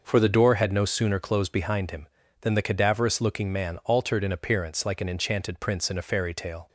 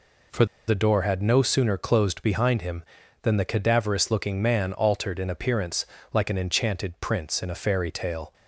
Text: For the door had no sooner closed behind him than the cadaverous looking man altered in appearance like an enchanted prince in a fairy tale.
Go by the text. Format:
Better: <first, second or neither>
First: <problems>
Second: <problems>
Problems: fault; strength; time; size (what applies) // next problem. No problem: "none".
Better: first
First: none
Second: pauses between "For" and "the"; slight; at 0.4 s; 0.22 s long // pauses between "appearance" and "like"; slight; at 5.8 s; 0.28 s long